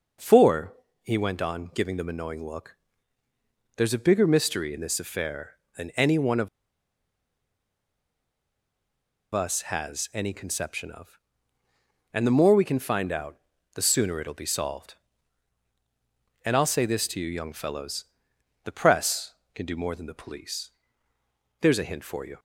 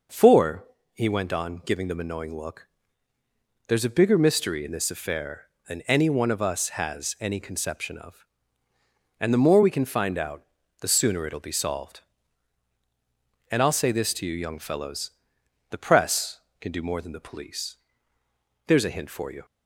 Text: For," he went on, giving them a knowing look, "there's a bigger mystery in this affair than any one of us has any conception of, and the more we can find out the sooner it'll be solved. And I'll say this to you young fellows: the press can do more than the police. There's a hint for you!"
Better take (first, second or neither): second